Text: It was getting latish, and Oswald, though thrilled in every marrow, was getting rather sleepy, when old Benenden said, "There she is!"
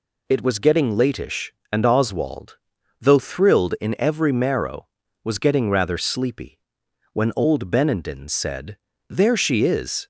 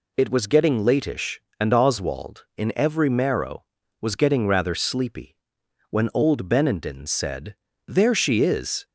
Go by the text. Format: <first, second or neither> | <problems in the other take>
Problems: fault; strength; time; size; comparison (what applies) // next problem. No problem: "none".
first | skips "though thrilled"; at 2.5 s